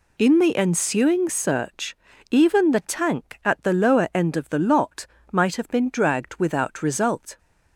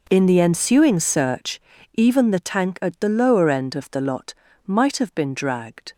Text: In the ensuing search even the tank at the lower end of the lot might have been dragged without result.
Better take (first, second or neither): first